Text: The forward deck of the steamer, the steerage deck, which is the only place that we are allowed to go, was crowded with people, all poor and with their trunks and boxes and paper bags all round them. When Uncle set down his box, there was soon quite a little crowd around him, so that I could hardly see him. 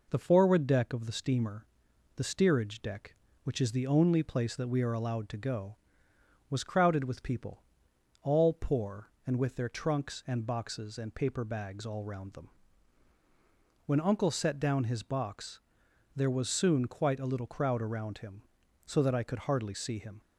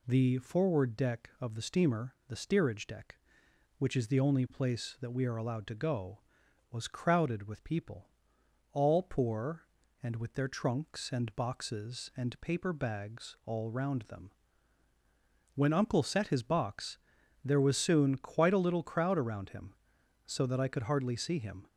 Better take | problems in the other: first | skips "down"; at 16.2 s

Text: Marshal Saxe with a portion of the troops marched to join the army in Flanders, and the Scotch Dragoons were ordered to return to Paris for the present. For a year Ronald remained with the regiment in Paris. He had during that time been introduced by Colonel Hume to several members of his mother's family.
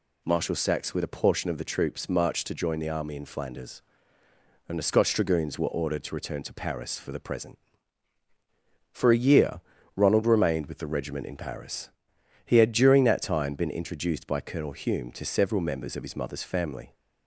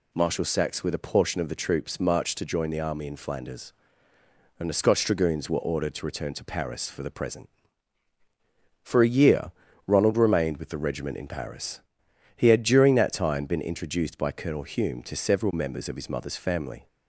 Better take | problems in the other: neither | pauses between "year" and "Ronald"; slight; the same in both

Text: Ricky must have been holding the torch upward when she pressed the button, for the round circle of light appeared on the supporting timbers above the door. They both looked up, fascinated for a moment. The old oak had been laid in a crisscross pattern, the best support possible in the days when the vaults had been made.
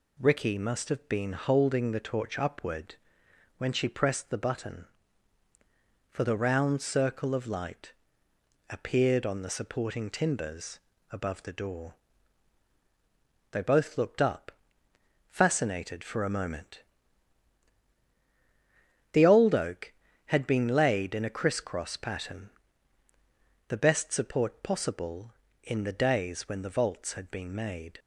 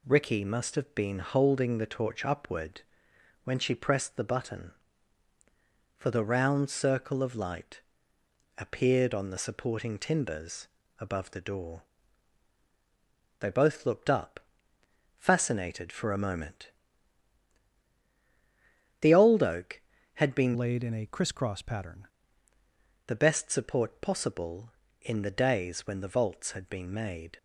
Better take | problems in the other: first | pauses between "upward" and "when"; noticeable; at 2.8 s; 0.62 s long; noticeable in the first // pauses between "light" and "appeared"; noticeable; at 7.8 s; 0.76 s long; noticeable in the first // pauses between "timbers" and "above"; slight; at 10.6 s; 0.32 s long; slight in the first // changes voice from "laid" to "pattern"; from 20.5 to 22.0 s; 1.5 s long

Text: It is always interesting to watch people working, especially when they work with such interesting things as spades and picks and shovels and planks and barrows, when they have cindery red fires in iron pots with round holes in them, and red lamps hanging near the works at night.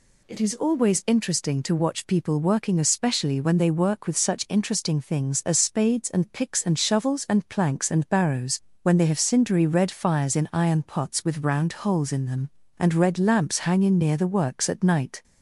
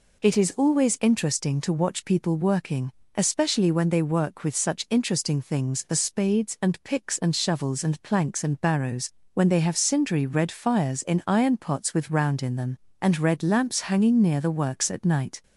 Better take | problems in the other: first | skips "holes"; at 12.4 s

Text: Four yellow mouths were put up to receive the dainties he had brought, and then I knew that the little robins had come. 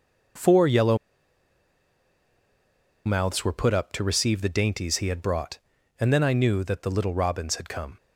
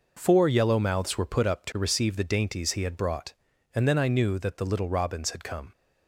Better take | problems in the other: second | pauses between "yellow" and "mouths"; strong; at 0.9 s; 2.0 s long

